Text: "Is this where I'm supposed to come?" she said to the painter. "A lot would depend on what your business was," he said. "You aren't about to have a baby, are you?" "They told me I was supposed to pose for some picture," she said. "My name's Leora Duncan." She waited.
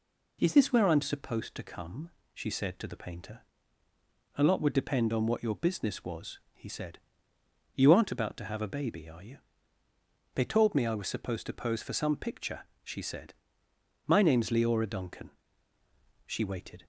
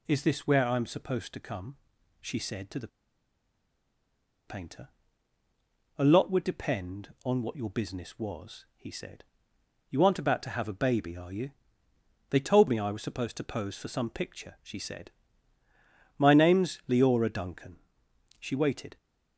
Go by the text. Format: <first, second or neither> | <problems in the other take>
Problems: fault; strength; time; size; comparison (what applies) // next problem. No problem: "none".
first | pauses between "the" and "painter"; strong; at 2.8 s; 1.6 s long